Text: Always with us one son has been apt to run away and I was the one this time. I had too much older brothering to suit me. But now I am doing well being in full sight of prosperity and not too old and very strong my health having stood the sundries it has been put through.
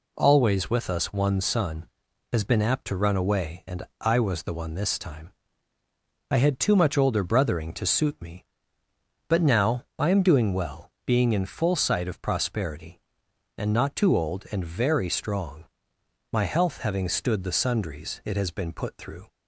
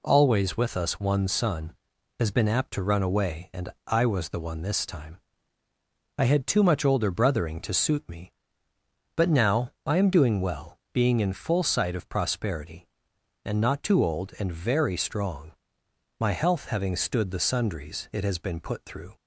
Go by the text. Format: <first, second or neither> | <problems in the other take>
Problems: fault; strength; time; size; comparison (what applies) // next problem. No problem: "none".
neither | pauses between "and" and "I"; slight; the same in both // pauses between "well" and "being"; slight; the same in both // pauses between "strong" and "my"; noticeable; the same in both